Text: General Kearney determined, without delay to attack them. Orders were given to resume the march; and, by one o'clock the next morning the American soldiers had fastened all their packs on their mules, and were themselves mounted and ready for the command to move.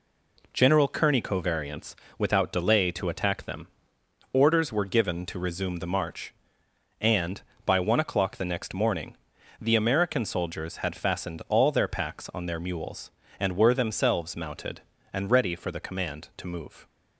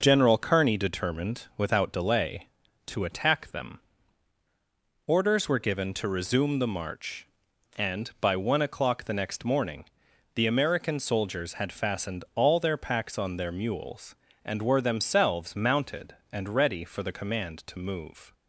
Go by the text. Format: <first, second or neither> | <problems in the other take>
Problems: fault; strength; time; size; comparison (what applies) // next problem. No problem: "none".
second | says "covariants" for "determined"; at 1.2 s // pauses between "morning" and "the"; noticeable; at 9.1 s; 0.46 s long; noticeable in the second